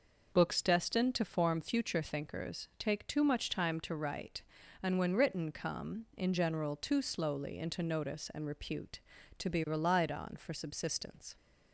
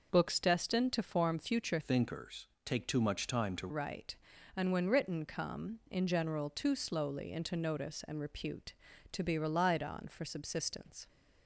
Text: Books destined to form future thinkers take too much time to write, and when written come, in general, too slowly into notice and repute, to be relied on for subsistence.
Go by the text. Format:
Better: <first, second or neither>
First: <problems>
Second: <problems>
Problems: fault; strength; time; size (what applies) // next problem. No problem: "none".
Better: first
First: none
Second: changes voice from "thinkers" to "to"; from 1.8 to 3.6 s; 1.8 s long // pauses between "thinkers" and "take"; slight; at 2.4 s; 0.16 s long